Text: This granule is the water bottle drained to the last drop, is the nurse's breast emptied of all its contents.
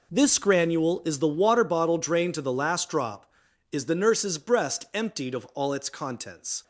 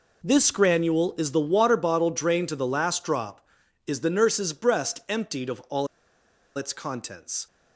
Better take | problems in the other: first | pauses between "all" and "its"; noticeable; at 5.8 s; 0.69 s long

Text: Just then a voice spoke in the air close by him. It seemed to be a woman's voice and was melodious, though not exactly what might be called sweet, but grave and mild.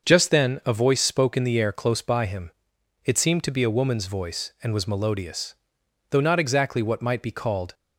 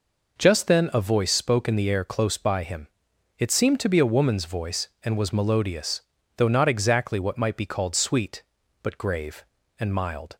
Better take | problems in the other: second | starts louder than the rest; until 1.1 s; 6.5 dB // stops before "sweet but grave and mild"; at 7.7 s

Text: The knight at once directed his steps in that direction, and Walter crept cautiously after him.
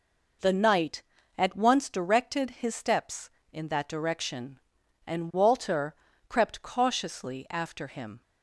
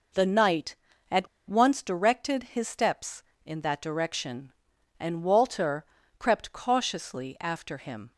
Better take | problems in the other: first | pauses between "at" and "once"; slight; at 1.2 s; 0.22 s long // pauses between "Walter" and "crept"; slight; at 5.8 s; 0.34 s long; slight in the first

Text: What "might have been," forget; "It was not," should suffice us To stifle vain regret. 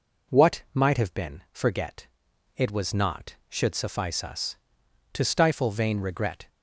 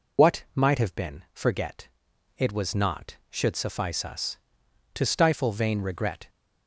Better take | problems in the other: first | loses the start of "What"; at 0.1 s; 75 ms

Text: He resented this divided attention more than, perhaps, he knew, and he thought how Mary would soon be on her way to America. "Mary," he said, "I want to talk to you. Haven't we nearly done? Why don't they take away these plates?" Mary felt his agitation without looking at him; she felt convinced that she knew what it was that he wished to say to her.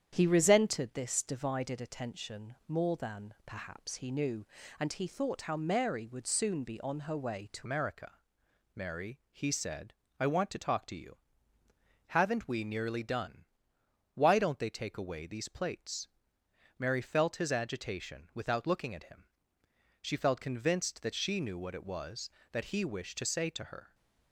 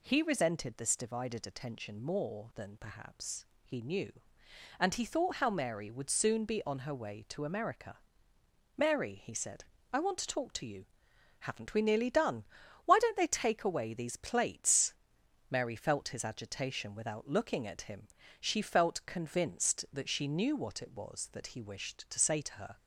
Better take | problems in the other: second | starts louder than the rest; strong; until 1.1 s; 9 dB // changes voice at "America"; from 7.6 s on; 16.3 s long

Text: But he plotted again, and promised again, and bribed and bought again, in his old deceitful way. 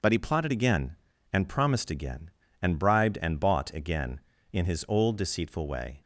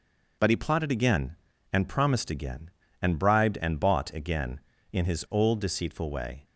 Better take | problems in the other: neither | none

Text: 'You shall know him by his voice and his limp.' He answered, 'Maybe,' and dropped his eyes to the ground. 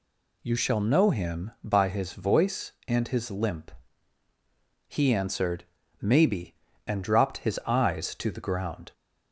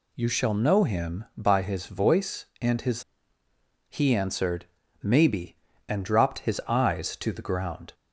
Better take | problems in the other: first | skips "limp"; at 3.4 s

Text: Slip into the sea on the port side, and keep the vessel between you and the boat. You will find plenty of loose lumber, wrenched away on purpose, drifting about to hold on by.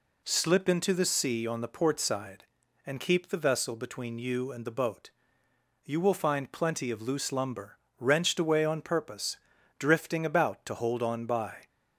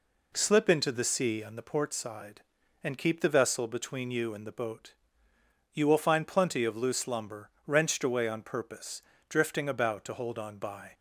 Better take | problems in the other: neither | none

